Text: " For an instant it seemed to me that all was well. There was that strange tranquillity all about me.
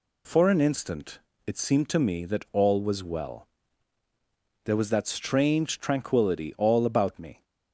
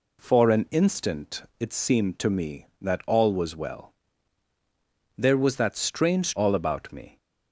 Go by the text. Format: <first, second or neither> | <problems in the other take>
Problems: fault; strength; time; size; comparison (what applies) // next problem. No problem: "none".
first | pauses between "instant" and "it"; slight; at 1.4 s; 0.16 s long; slight in the first // skips "tranquillity"; at 6.3 s